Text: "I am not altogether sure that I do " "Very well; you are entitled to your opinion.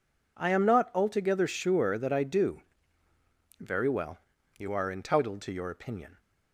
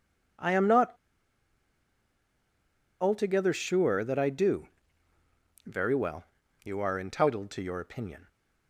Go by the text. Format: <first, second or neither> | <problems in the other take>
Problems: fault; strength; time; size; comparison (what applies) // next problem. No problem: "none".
first | pauses between "not" and "altogether"; strong; at 0.9 s; 2.0 s long